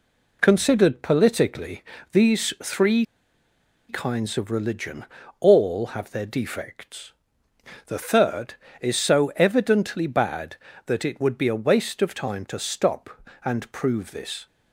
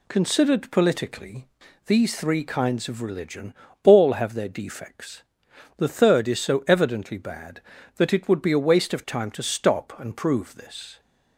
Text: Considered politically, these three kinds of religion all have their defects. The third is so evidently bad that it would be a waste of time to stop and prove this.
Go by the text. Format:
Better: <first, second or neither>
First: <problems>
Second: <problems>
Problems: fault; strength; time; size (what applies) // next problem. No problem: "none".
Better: second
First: pauses between "three" and "kinds"; noticeable; at 3.0 s; 0.84 s long // pauses between "religion" and "all"; slight; at 5.0 s; 0.34 s long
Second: pauses between "religion" and "all"; slight; at 3.5 s; 0.30 s long